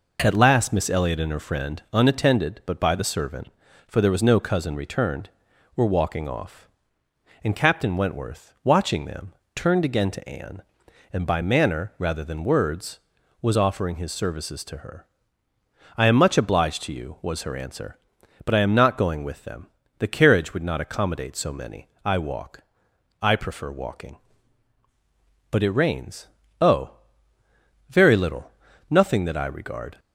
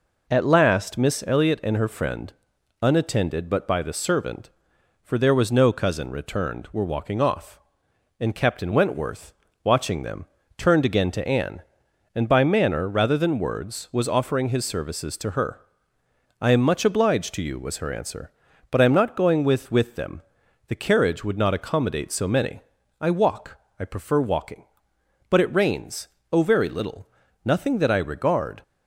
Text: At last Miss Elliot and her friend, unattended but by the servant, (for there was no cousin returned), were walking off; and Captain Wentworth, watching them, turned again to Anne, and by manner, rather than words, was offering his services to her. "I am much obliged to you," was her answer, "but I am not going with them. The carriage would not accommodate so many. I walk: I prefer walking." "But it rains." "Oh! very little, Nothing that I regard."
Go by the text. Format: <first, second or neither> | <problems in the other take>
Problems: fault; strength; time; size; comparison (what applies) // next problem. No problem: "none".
first | says "with" twice; at 19.7 s